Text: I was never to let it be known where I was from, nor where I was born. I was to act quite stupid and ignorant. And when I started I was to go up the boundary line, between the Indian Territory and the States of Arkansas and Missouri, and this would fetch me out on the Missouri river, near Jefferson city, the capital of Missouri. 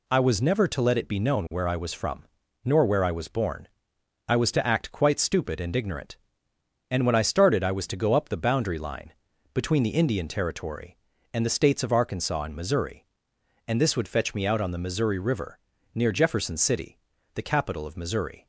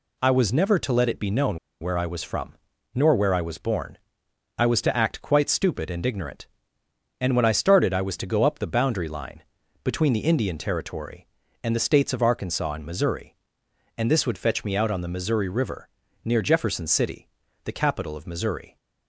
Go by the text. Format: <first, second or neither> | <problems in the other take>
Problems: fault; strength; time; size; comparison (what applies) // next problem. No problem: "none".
first | pauses between "known" and "where"; slight; at 1.5 s; 0.23 s long